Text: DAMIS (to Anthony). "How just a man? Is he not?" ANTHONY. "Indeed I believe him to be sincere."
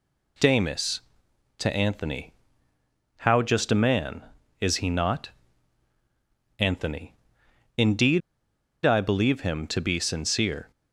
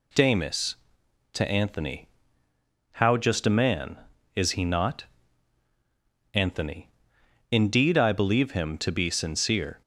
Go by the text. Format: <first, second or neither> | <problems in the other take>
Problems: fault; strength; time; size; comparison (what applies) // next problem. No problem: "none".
second | pauses between "Indeed" and "I"; noticeable; at 8.2 s; 0.63 s long